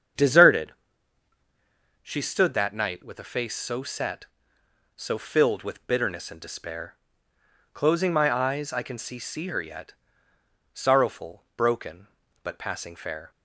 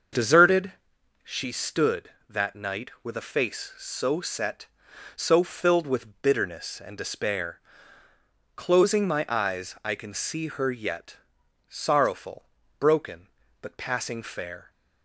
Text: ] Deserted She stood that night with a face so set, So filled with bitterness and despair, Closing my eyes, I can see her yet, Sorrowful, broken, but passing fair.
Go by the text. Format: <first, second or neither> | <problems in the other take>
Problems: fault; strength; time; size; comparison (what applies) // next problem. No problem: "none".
second | starts louder than the rest; strong; until 2.4 s; 7.5 dB; also in the second // pauses between "Deserted" and "She"; strong; at 0.7 s; 1.3 s long; noticeable in the second // says "see" twice; at 9.1 s